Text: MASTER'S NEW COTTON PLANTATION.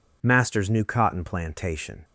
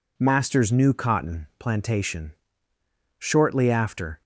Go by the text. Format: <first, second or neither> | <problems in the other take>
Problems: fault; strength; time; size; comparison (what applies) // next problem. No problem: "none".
first | goes on to say "Shortly after"; noticeable; from 3.1 s on; 1.0 s long